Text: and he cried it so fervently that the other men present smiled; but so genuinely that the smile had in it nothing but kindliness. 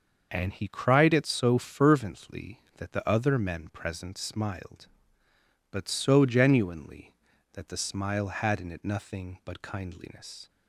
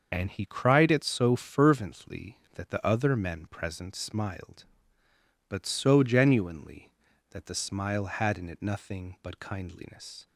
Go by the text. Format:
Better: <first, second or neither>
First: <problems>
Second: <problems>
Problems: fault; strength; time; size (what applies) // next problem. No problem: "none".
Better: first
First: starts louder than the rest; until 1.3 s; 6.5 dB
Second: loses the start of "and"; at 0.1 s; 30 ms // starts louder than the rest; until 1.1 s; 6.5 dB